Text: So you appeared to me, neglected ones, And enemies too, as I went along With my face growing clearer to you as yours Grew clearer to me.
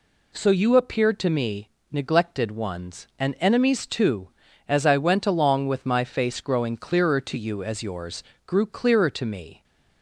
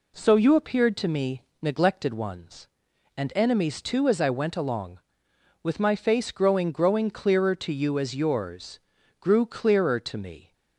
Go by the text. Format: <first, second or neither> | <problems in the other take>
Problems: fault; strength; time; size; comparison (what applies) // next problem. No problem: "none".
first | says "growing" twice; at 6.7 s // pauses between "yours" and "Grew"; at 8.7 s; 0.40 s long; slight in the first